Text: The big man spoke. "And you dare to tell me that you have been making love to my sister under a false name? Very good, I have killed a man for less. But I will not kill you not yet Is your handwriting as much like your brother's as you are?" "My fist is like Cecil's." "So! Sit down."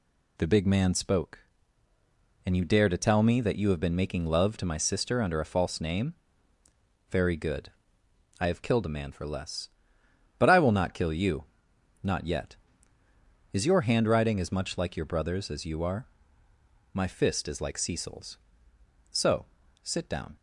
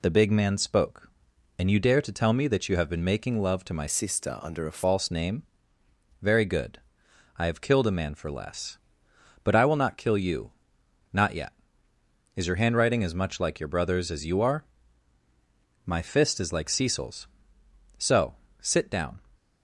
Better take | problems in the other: first | changes voice from "sister" to "a"; from 3.8 to 4.8 s; 1.0 s long // pauses between "you" and "not"; noticeable; at 10.5 s; 0.60 s long; noticeable in the first

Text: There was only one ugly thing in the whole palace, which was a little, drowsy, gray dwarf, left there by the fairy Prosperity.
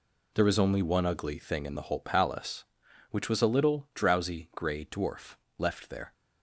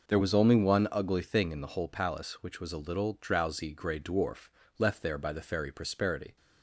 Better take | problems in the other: second | stops before "by the fairy Prosperity"; at 6.1 s

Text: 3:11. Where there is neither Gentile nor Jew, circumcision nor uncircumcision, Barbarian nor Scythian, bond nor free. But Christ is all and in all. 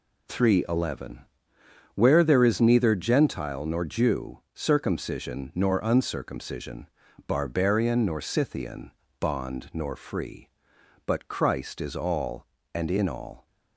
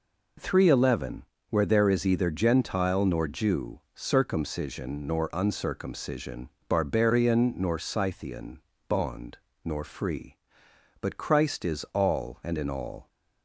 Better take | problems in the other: first | says "either" for "neither"; at 2.0 s // pauses between "bond" and "nor"; slight; at 9.3 s; 0.26 s long

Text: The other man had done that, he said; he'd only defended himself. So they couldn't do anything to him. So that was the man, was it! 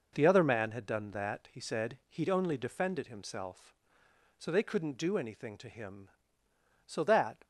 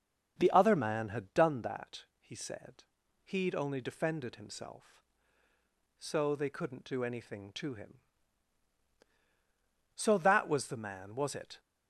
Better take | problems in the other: second | stops before "was the man was it"; at 7.4 s

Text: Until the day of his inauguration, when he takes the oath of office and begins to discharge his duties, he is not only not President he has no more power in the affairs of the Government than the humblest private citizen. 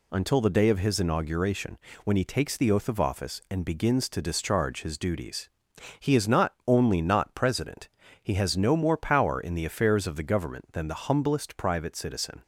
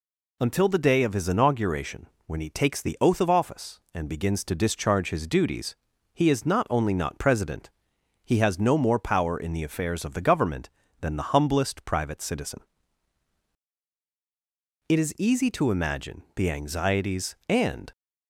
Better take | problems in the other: first | pauses between "President" and "he"; noticeable; at 7.7 s; 0.54 s long; slight in the first // goes on to say "It is easy to imagine the anxieties and"; strong; from 14.8 s on; 3.0 s long

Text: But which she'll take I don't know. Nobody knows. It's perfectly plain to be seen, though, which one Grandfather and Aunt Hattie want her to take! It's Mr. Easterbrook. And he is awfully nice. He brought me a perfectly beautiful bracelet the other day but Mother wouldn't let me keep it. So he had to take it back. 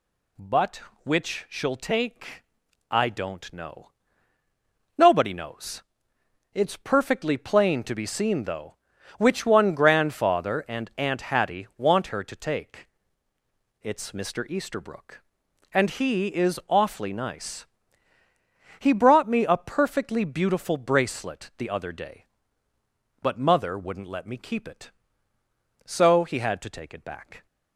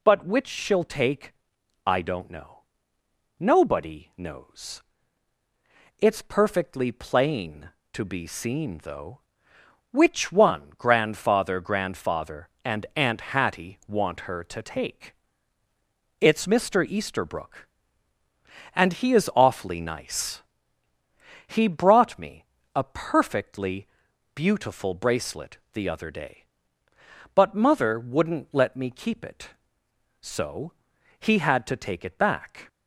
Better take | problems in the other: first | pauses between "take" and "I"; noticeable; at 1.3 s; 0.54 s long; noticeable in the first // says "Grandfather" twice; at 11.5 s // pauses between "me" and "a"; slight; at 22.4 s; 0.28 s long // pauses between "perfectly" and "beautiful"; noticeable; at 23.8 s; 0.48 s long // pauses between "bracelet" and "the"; slight; at 25.5 s; 0.16 s long // pauses between "So" and "he"; at 30.7 s; 0.44 s long

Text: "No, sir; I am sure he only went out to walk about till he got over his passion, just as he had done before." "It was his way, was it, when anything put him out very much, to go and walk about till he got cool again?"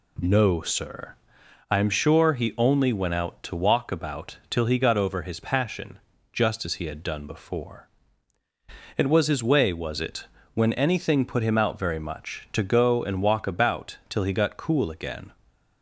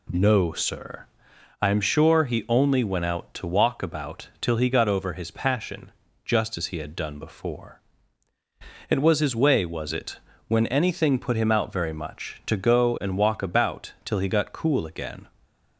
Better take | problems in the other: neither | none

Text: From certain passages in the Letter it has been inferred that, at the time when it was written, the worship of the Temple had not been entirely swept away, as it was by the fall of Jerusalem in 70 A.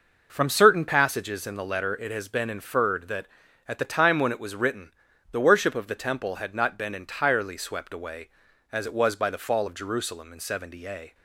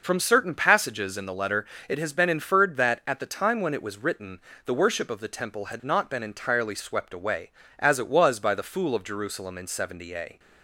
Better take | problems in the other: first | pauses between "Letter" and "it"; slight; at 1.6 s; 0.24 s long // says "fool" for "fall"; at 8.6 s

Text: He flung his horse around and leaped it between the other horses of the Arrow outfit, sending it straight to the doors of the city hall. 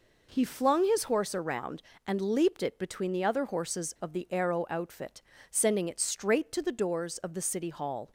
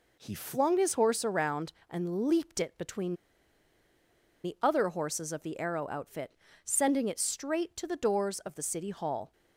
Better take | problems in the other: first | pauses between "between" and "the"; strong; at 3.1 s; 1.3 s long

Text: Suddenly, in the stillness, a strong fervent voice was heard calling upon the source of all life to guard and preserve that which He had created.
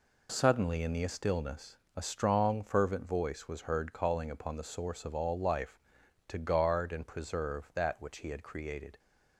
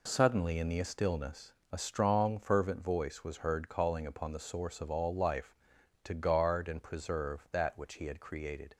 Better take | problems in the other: neither | none

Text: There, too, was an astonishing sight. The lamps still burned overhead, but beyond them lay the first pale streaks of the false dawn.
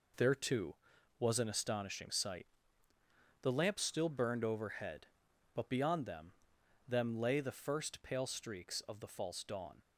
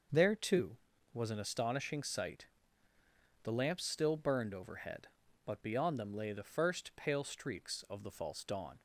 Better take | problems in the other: second | says "them" twice; at 6.8 s

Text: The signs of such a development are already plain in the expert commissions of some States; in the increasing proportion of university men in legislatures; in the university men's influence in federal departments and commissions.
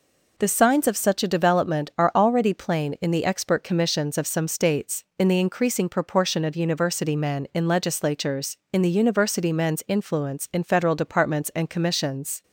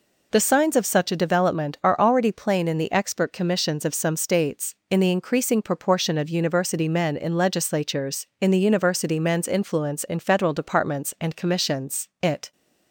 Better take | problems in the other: first | goes on to say "It"; slight; from 12.2 s on; 0.30 s long

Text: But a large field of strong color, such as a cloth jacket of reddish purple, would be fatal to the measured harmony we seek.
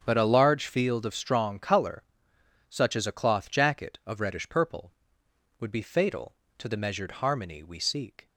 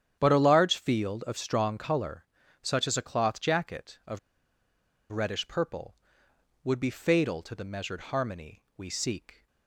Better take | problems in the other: first | starts louder than the rest; strong; until 1.2 s; 9.5 dB; strong in the first // pauses between "of" and "reddish"; noticeable; at 4.1 s; 0.93 s long

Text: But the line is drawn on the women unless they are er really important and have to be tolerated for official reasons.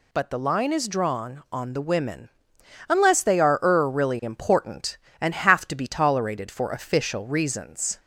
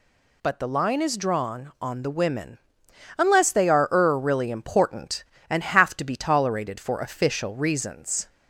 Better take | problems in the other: neither | pauses between "women" and "unless"; noticeable; the same in both

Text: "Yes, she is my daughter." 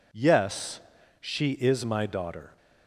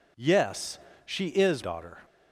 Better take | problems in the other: first | skips "my"; at 1.6 s

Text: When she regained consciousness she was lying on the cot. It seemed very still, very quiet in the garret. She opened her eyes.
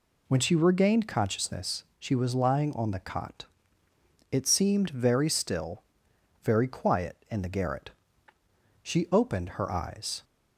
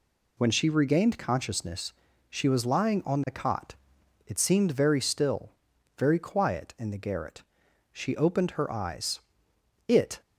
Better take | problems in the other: first | pauses between "consciousness" and "she"; at 1.9 s; 0.38 s long; slight in the first // goes on to say "It"; slight; from 9.8 s on; 0.32 s long

